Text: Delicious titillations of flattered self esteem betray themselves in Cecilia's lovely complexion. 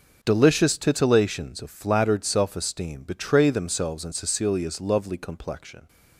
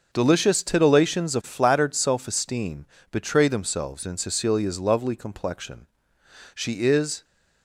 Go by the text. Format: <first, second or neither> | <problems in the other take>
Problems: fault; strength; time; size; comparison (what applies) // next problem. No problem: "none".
first | starts louder than the rest; until 1.1 s; 6.5 dB // pauses between "esteem" and "betray"; slight; at 2.8 s; 0.24 s long // goes on to say "She is"; noticeable; from 6.5 s on; 0.70 s long